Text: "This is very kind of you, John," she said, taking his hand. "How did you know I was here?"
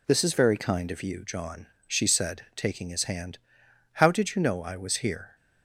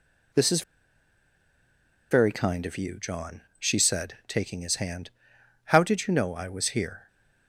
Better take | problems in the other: first | pauses between "is" and "very"; strong; at 0.6 s; 1.4 s long

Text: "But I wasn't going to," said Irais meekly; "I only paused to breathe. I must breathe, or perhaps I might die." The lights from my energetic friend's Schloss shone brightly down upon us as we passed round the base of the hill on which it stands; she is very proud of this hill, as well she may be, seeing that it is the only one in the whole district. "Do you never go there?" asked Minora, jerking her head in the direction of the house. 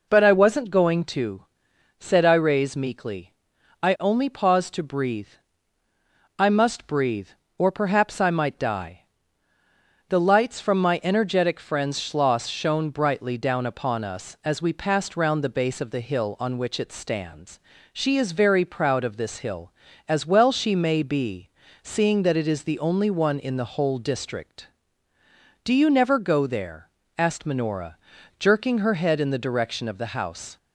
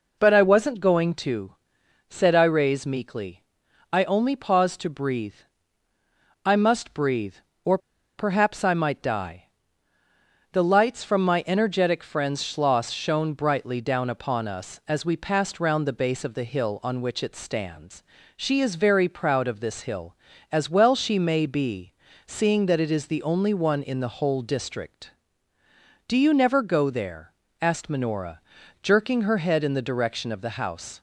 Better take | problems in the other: first | pauses between "or" and "perhaps"; at 7.7 s; 0.39 s long

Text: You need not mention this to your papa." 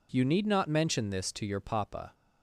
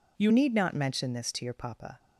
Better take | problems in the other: first | changes voice at "need"; from 0.2 s on; 1.7 s long

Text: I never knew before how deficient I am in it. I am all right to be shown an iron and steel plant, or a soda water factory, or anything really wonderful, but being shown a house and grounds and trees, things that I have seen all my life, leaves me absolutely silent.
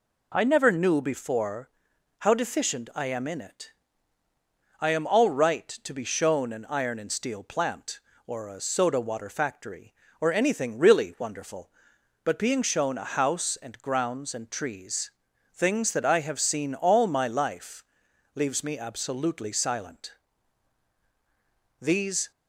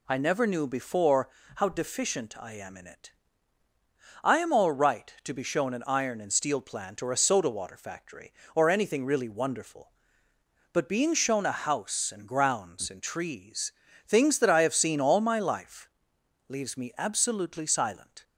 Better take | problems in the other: second | pauses between "before" and "how"; noticeable; at 1.6 s; 0.52 s long; slight in the second // goes on to say "These"; from 21.7 s on; 0.52 s long

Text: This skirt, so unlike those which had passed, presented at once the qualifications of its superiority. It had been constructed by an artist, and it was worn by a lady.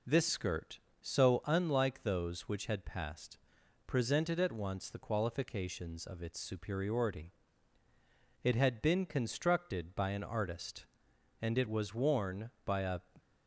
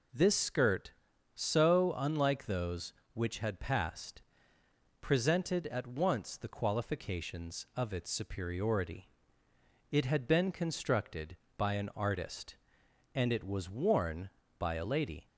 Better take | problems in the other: second | stops before "lady"; at 13.1 s

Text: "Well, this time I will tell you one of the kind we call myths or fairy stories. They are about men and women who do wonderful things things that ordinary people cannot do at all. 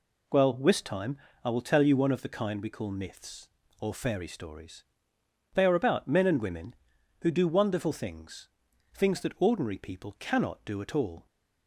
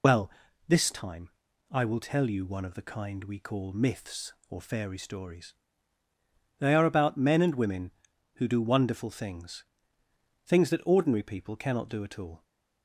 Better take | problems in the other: first | loses the start of "Well"; at 0.0 s; 40 ms // pauses between "time" and "I"; at 1.2 s; 0.44 s long; slight in the first // pauses between "things" and "things"; noticeable; at 9.6 s; 0.80 s long; also in the first

